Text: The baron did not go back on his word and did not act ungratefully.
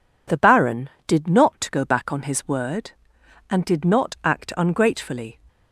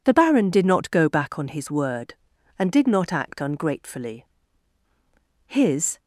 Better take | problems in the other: first | goes on to say "His"; from 5.4 s on; 0.54 s long

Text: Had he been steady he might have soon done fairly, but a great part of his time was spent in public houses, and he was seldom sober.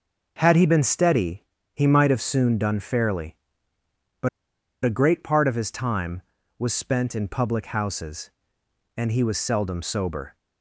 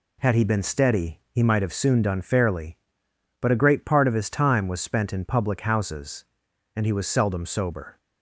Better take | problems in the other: second | pauses between "steady" and "he"; slight; at 1.4 s; 0.32 s long // pauses between "but" and "a"; noticeable; at 4.2 s; 0.55 s long

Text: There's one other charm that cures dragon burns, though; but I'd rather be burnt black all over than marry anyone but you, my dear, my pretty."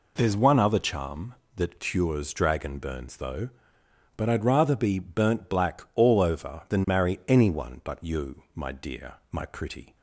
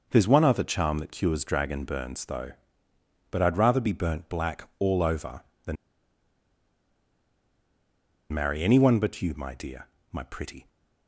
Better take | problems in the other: first | pauses between "than" and "marry"; strong; at 5.7 s; 2.5 s long

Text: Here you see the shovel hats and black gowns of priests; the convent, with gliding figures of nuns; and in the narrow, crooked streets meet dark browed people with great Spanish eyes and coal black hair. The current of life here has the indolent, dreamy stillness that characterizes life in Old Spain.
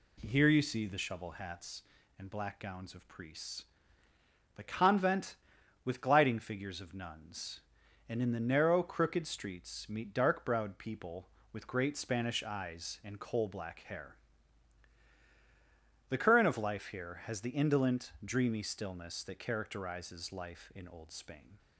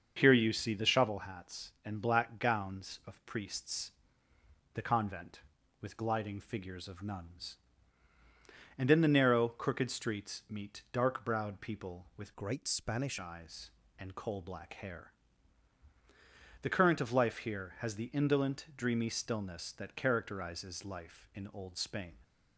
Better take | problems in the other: first | starts louder than the rest; until 1.1 s; 6.5 dB // changes voice from "great" to "Spanish"; from 12.3 to 13.1 s; 0.8 s long

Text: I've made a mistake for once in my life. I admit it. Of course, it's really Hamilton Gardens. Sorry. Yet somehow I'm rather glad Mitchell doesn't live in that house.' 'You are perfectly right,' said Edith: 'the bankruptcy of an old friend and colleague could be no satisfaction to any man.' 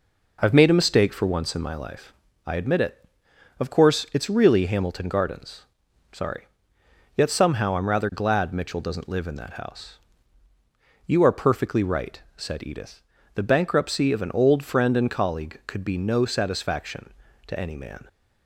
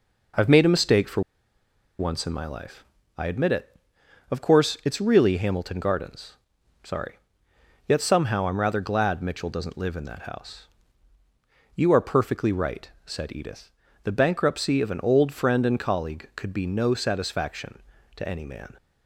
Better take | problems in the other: first | pauses between "for" and "once"; noticeable; at 1.2 s; 0.78 s long

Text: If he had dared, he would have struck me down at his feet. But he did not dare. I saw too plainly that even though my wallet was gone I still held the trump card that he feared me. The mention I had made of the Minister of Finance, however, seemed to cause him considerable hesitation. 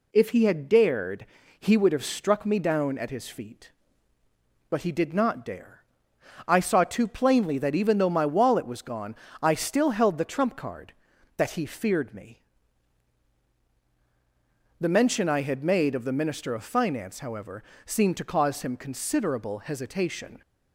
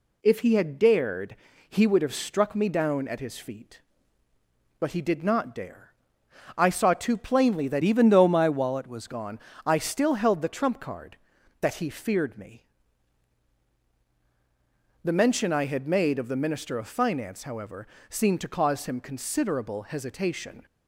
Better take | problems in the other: first | changes voice from "even" to "was"; from 7.8 to 9.0 s; 1.2 s long // pauses between "gone" and "I"; slight; at 9.3 s; 0.28 s long; slight in the first

